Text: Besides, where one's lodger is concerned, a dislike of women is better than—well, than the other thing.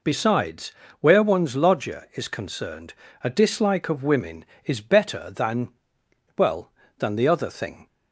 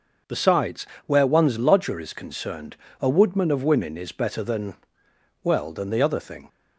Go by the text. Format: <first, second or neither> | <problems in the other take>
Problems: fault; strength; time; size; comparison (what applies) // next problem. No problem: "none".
first | starts louder than the rest; until 1.4 s; 6 dB // says "woodman" for "dislike"; at 3.0 s